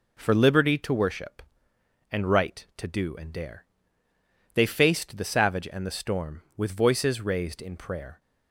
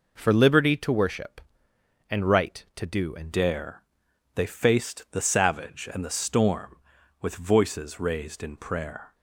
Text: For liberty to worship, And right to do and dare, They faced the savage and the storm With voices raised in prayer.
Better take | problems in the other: first | changes voice at "dare"; from 3.3 s on; 5.8 s long

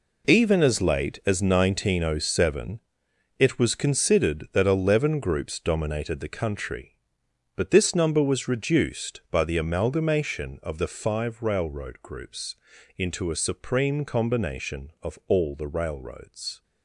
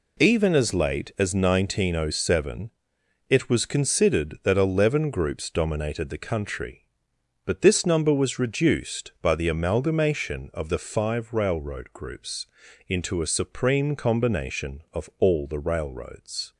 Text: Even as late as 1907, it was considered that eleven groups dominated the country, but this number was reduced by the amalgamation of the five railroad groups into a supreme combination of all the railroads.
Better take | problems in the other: second | gets quieter; strong; throughout; 12 dB // pauses between "groups" and "into"; at 12.5 s; 0.40 s long; also in the second

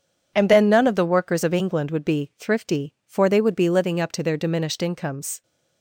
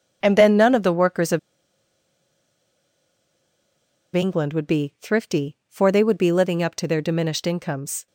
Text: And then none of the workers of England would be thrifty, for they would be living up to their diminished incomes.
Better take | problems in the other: first | pauses between "of" and "England"; strong; at 1.3 s; 2.7 s long

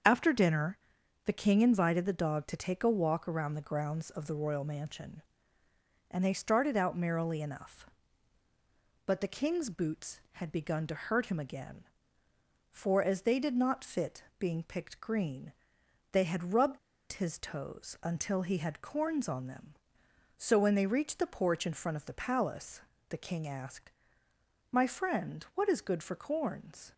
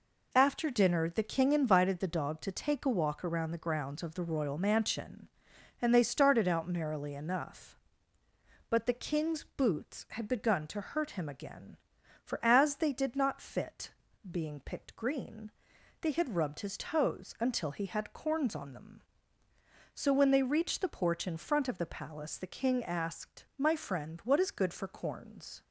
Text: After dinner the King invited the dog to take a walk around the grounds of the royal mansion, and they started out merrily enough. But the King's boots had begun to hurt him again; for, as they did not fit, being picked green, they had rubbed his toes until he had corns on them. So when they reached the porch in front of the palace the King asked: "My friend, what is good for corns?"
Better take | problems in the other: second | starts louder than the rest; strong; until 1.5 s; 7 dB // pauses between "dinner" and "the"; noticeable; at 0.7 s; 0.48 s long // pauses between "rubbed" and "his"; slight; at 16.7 s; 0.34 s long // pauses between "palace" and "the"; slight; at 22.7 s; 0.30 s long

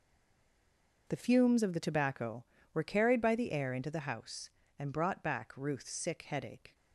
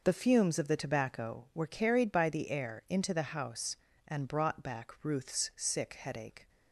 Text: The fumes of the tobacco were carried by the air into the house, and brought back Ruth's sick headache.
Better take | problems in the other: second | stays silent before the first word; until 1.0 s; 1.0 s long

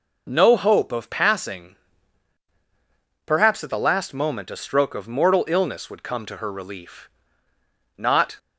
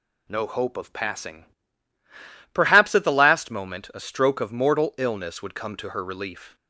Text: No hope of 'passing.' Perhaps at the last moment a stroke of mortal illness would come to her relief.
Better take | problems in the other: second | goes on to say "Not"; slight; from 7.9 s on; 0.42 s long

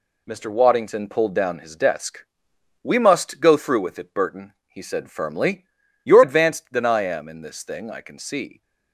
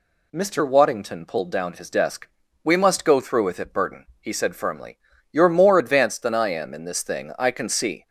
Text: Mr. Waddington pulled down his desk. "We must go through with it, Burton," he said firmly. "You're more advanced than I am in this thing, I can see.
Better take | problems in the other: second | skips "more"; at 6.2 s

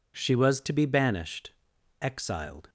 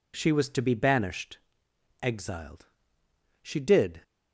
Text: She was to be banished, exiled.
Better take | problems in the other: first | goes on to say "She did"; from 3.4 s on; 0.60 s long

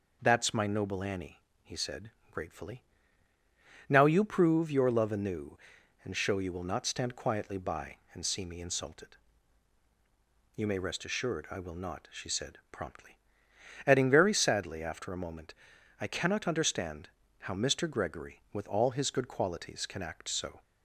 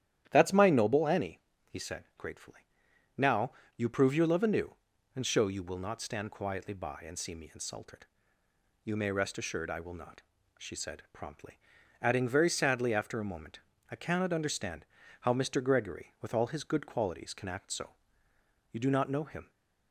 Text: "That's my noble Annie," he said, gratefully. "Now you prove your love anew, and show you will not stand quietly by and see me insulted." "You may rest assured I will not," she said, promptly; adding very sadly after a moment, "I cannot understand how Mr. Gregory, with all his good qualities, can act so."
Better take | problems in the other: first | starts louder than the rest; strong; until 1.3 s; 11 dB // pauses between "Now" and "you"; slight; at 3.5 s; 0.24 s long // pauses between "understand" and "how"; slight; at 14.8 s; 0.36 s long; slight in the first // goes on to say "You do not know him"; noticeable; from 18.7 s on; 0.78 s long

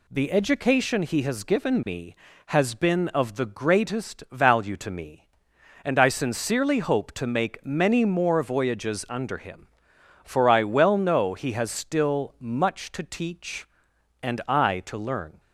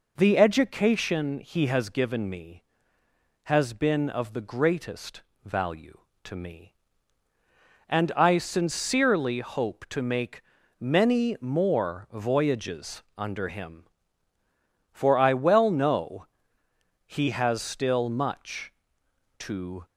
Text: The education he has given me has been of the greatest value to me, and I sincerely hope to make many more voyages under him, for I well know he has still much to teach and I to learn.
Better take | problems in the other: first | pauses between "greatest" and "value"; slight; at 5.2 s; 0.20 s long // pauses between "make" and "many"; at 10.4 s; 0.38 s long // pauses between "know" and "he"; noticeable; at 16.2 s; 0.82 s long // stops before "teach and I to learn"; at 19.8 s

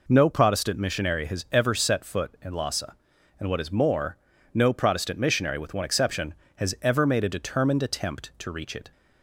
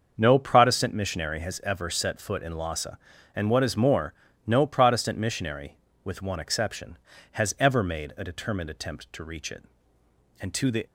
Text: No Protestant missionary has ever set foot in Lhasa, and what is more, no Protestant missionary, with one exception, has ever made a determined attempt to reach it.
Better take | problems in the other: first | starts louder than the rest; until 1.1 s; 6.5 dB // goes on to say "And to the"; slight; from 10.3 s on; 0.46 s long

